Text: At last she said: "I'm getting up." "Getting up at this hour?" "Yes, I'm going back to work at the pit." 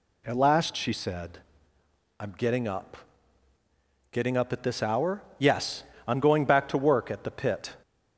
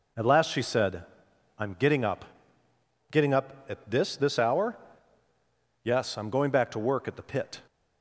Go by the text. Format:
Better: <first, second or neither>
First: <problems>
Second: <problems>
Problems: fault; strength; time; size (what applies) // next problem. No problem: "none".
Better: first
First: none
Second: says "this" twice; at 4.1 s